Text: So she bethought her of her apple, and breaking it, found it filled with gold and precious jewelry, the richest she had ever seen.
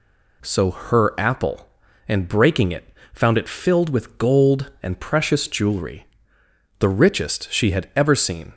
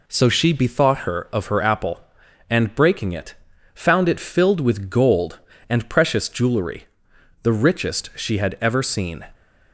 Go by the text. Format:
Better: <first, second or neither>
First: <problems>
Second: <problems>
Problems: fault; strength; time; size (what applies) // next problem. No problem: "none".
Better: second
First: skips "she bethought her of"; at 0.7 s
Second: none